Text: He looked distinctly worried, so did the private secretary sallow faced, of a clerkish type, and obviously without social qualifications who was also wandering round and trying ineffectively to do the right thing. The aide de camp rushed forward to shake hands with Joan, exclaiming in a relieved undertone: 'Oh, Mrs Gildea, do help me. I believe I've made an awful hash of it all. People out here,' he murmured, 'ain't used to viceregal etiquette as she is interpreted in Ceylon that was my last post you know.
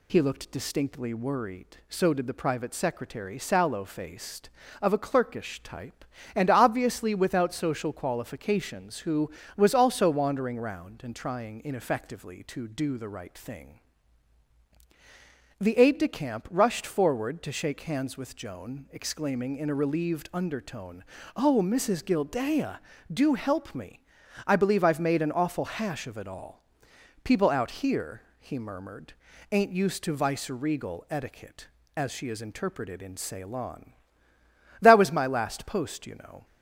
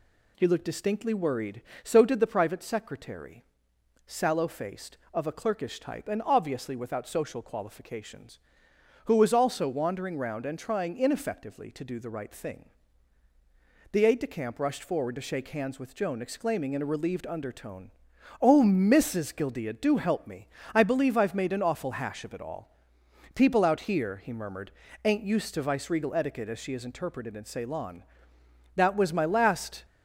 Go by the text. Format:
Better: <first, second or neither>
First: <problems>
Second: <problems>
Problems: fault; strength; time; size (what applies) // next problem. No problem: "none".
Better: first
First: none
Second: pauses between "secretary" and "sallow"; noticeable; at 3.4 s; 0.64 s long // stops before "post you know"; at 29.8 s